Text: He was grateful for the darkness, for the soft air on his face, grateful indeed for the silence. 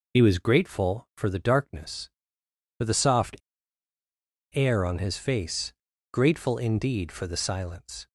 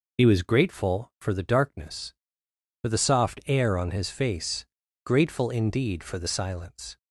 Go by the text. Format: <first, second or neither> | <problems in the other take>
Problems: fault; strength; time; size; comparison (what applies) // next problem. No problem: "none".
second | pauses between "soft" and "air"; at 3.3 s; 1.1 s long